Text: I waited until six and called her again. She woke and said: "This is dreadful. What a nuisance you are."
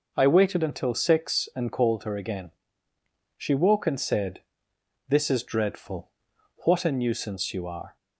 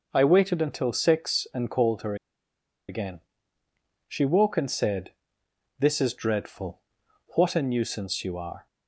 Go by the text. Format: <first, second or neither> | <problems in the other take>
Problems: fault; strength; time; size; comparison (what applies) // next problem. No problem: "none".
first | pauses between "her" and "again"; noticeable; at 2.1 s; 0.73 s long